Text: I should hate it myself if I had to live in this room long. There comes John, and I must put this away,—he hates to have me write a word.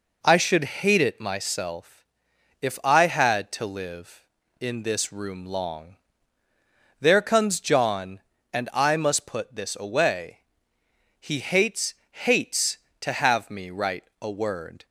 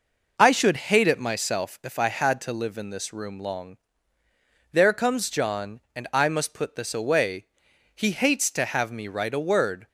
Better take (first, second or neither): second